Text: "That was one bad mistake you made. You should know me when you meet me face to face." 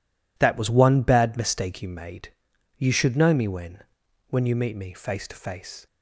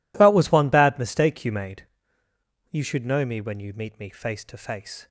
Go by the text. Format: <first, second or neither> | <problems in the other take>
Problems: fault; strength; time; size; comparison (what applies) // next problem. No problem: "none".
second | says "when" twice; at 4.2 s